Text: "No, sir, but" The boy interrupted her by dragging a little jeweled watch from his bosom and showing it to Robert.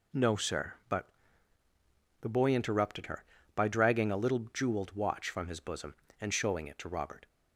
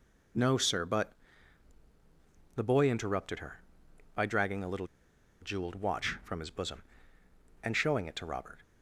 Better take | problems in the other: first | pauses between "but" and "The"; strong; at 1.1 s; 1.4 s long; also in the first // pauses between "little" and "jeweled"; noticeable; at 4.8 s; 0.55 s long

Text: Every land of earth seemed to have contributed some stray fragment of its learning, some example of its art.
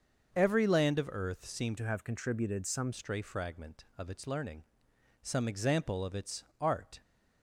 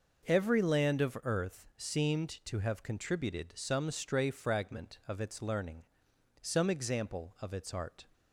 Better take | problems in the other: second | starts louder than the rest; until 1.3 s; 6.5 dB // changes voice from "to" to "some"; from 1.7 to 2.9 s; 1.2 s long // pauses between "its" and "art"; slight; at 6.4 s; 0.16 s long

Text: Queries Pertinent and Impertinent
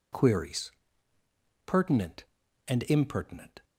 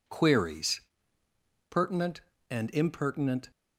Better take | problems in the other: neither | pauses between "Queries" and "Pertinent"; noticeable; the same in both

